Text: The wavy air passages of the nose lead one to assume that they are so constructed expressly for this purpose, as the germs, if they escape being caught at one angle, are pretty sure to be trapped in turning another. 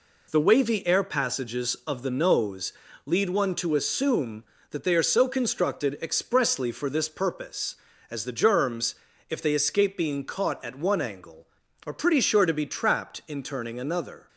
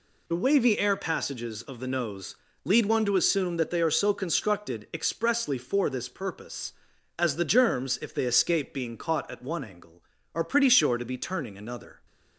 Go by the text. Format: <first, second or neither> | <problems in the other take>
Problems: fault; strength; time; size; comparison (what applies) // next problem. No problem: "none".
first | pauses between "nose" and "lead"; slight; at 2.3 s; 0.28 s long; slight in the first // skips "trapped in"; at 11.1 s